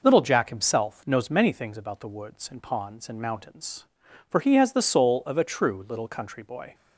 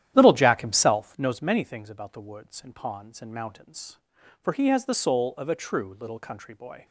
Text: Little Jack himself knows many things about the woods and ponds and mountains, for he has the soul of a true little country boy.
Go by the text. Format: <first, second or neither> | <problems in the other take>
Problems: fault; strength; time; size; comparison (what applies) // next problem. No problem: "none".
first | starts louder than the rest; strong; until 1.3 s; 11.5 dB